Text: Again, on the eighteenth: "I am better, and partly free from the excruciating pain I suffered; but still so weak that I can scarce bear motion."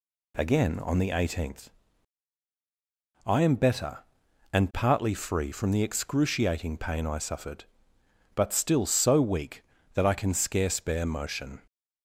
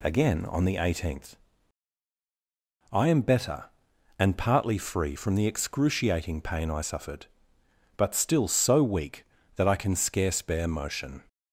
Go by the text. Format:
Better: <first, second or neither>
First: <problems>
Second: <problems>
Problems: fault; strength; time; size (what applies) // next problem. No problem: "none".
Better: neither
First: none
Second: none